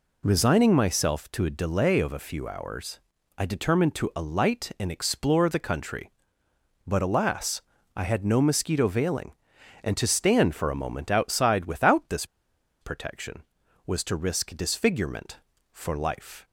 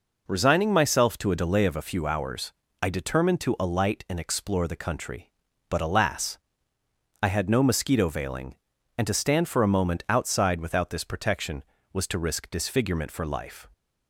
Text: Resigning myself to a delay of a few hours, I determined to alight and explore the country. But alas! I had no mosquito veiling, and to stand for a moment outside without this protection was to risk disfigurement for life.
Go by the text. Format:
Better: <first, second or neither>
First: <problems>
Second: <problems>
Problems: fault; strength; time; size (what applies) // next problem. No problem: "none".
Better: second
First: pauses between "this" and "protection"; noticeable; at 12.2 s; 0.57 s long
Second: none